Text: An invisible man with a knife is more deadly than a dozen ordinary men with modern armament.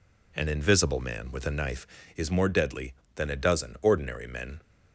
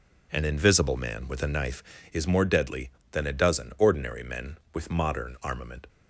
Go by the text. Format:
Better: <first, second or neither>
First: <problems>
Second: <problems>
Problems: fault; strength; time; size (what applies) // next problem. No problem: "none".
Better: second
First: stops before "with modern armament"; at 4.6 s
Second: none